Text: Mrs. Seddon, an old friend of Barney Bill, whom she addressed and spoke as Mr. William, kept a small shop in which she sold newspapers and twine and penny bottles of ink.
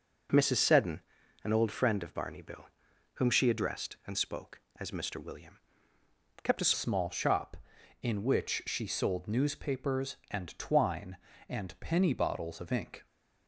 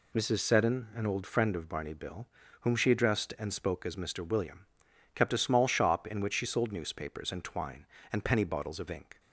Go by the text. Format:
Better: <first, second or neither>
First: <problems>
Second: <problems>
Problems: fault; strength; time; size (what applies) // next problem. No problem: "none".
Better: second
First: changes voice at "small"; from 6.7 s on; 6.3 s long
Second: none